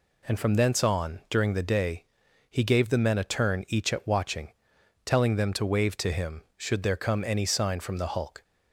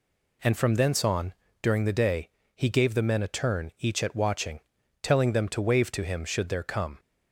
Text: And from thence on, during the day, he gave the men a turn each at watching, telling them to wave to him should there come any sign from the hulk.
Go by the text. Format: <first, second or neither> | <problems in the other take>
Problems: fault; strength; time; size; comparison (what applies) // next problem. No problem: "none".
first | stops before "any sign from the hulk"; at 6.9 s